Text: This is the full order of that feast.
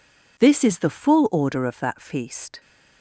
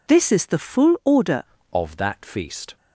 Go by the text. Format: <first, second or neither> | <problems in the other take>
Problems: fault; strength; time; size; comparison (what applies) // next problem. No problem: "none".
first | changes voice at "of"; from 1.7 s on; 1.0 s long